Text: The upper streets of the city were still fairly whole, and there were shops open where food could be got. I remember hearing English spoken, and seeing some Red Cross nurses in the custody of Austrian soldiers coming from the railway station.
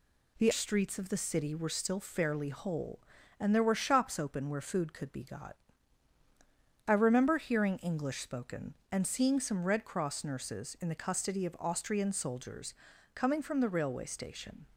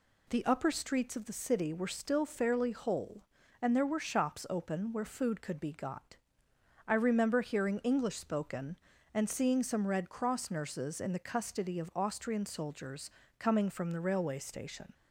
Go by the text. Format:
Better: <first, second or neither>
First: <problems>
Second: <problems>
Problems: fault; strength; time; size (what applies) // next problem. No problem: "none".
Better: second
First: skips "upper"; at 0.5 s // pauses between "soldiers" and "coming"; at 12.7 s; 0.42 s long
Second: pauses between "soldiers" and "coming"; slight; at 13.0 s; 0.30 s long